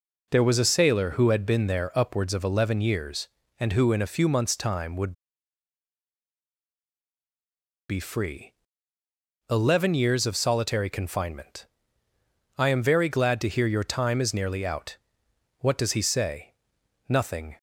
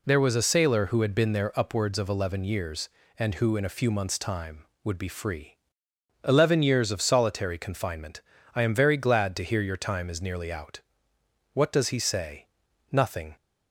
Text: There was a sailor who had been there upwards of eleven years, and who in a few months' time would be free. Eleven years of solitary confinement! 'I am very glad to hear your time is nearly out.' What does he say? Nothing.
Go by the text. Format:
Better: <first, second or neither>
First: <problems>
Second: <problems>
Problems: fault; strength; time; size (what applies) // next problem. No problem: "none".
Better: second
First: pauses between "would" and "be"; strong; at 5.1 s; 2.7 s long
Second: none